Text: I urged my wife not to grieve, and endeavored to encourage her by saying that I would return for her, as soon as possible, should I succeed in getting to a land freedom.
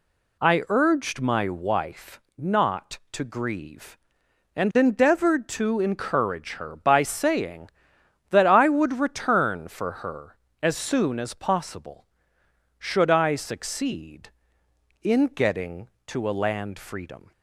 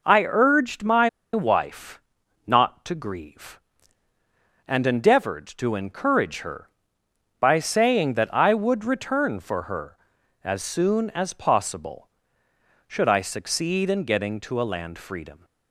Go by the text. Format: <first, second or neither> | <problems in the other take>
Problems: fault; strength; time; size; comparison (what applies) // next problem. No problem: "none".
first | pauses between "my" and "wife"; slight; at 1.0 s; 0.25 s long // pauses between "wife" and "not"; noticeable; at 2.0 s; 0.46 s long; slight in the first